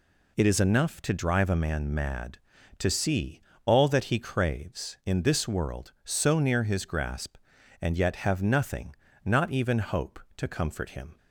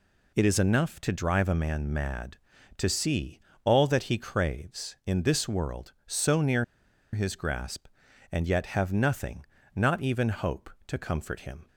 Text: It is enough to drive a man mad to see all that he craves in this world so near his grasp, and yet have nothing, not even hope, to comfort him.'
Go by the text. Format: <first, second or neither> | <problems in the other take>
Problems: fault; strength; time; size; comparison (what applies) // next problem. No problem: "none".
first | pauses between "see" and "all"; slight; at 3.3 s; 0.26 s long; slight in the first // pauses between "near" and "his"; noticeable; at 6.6 s; 0.48 s long